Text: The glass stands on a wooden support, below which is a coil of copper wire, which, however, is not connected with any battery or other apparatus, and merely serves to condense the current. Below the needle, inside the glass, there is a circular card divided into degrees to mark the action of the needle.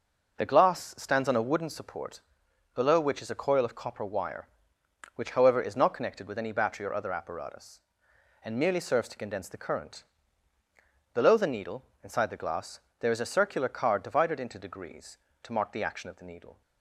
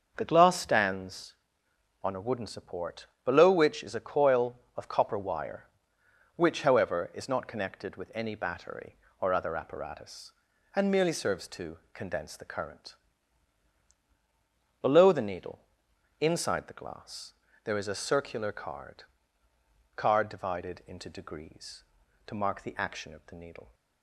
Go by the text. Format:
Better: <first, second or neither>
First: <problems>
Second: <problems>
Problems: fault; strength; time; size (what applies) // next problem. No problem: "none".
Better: first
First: none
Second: starts louder than the rest; until 1.1 s; 6.5 dB // pauses between "to" and "condense"; slight; at 11.7 s; 0.16 s long // says "card" twice; at 19.9 s